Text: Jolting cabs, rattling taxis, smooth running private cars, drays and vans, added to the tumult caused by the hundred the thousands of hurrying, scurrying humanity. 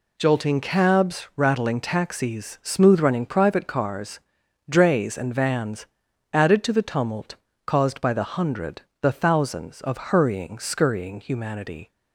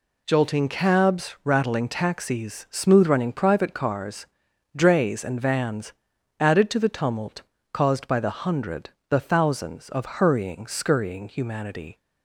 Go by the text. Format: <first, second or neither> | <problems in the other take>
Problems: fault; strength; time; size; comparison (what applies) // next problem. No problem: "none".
neither | pauses between "tumult" and "caused"; slight; the same in both // pauses between "hundred" and "the"; slight; the same in both